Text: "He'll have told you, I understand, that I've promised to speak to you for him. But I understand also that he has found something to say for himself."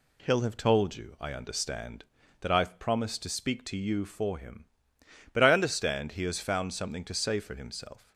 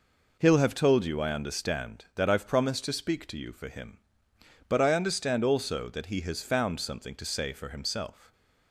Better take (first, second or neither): second